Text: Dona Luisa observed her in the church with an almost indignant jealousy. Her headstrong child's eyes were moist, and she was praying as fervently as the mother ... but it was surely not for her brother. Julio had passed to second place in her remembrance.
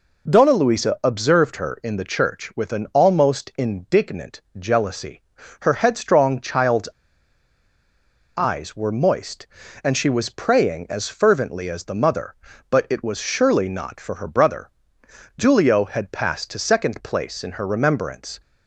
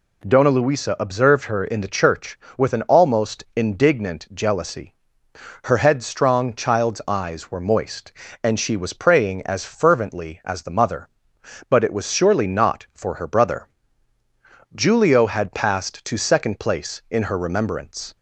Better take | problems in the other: second | pauses between "indignant" and "jealousy"; slight; at 4.4 s; 0.18 s long // pauses between "child's" and "eyes"; strong; at 6.8 s; 1.5 s long

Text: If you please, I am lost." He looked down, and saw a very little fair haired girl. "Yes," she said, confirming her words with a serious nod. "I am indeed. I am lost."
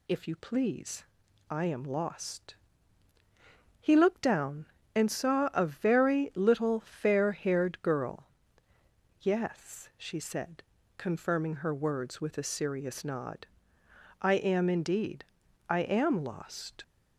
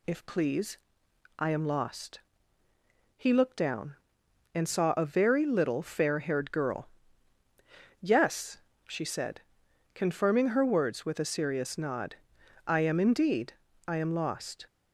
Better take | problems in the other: first | skips "you"; at 0.2 s

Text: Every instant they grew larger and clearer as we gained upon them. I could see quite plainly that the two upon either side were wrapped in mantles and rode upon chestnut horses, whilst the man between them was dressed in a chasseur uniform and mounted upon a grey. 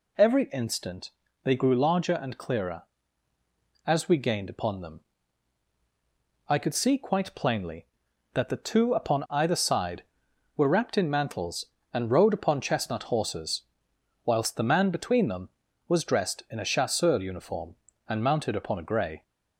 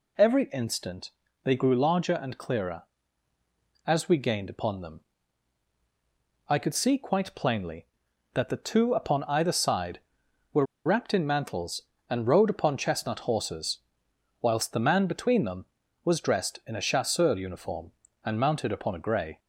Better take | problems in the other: first | pauses between "instant" and "they"; slight; at 1.0 s; 0.34 s long; slight in the first // pauses between "were" and "wrapped"; slight; at 10.6 s; 0.20 s long

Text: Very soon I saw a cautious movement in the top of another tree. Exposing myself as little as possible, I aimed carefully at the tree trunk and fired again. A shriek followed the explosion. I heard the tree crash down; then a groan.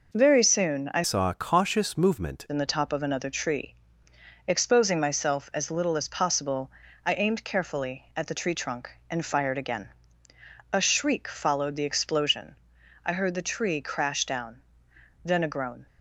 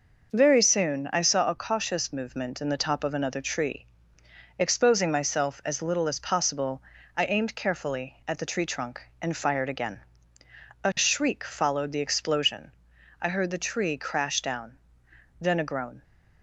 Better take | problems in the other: second | changes voice from "saw" to "movement"; from 1.0 to 2.4 s; 1.4 s long

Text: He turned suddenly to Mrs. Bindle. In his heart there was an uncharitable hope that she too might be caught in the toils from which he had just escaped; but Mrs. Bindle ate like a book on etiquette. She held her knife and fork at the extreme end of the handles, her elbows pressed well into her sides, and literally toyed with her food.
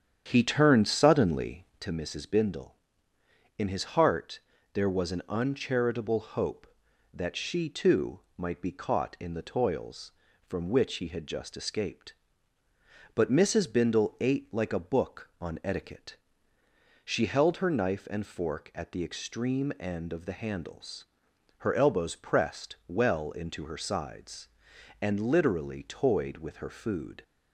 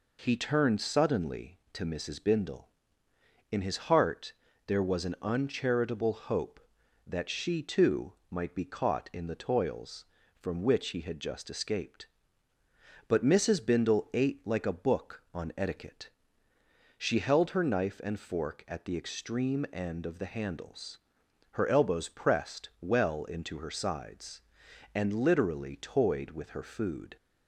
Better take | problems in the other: second | starts louder than the rest; strong; until 1.8 s; 8.5 dB // pauses between "heart" and "there"; slight; at 4.4 s; 0.32 s long; slight in the second // pauses between "too" and "might"; slight; at 8.1 s; 0.18 s long; slight in the second

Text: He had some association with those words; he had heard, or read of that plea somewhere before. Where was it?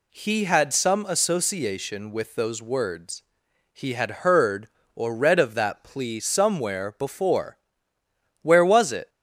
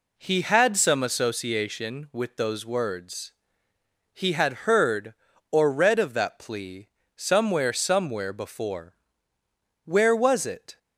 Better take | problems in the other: first | pauses between "plea" and "somewhere"; slight; at 6.8 s; 0.28 s long // says "somewhere" twice; at 7.7 s

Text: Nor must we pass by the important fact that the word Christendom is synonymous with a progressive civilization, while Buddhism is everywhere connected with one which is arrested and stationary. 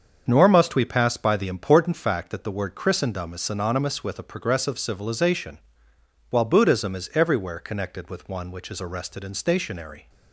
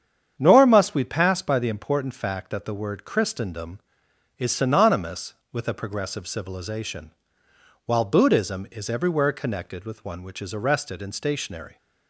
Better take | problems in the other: neither | starts louder than the rest; the same in both

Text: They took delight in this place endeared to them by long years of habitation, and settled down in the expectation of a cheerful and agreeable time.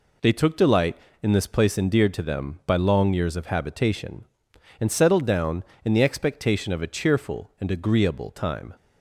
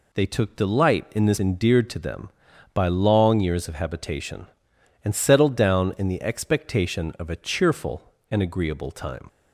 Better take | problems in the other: first | skips "place"; at 1.3 s

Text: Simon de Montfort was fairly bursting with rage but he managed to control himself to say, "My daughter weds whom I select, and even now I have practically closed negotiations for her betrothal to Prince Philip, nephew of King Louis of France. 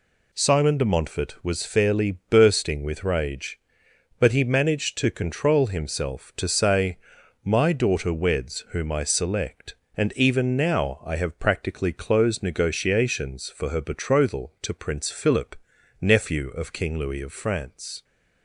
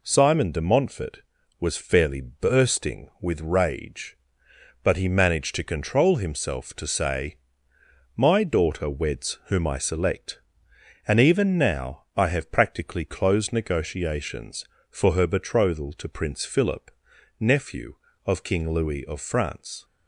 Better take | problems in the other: neither | none

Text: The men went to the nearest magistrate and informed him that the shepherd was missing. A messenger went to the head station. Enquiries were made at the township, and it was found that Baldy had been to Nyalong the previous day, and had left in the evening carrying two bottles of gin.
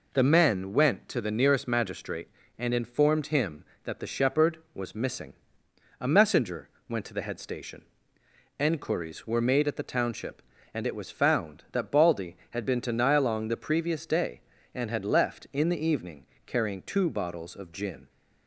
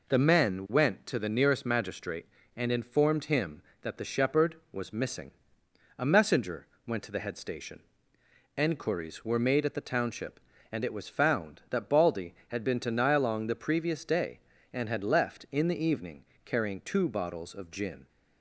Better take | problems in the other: neither | pauses between "messenger" and "went"; slight; the same in both // pauses between "evening" and "carrying"; slight; the same in both

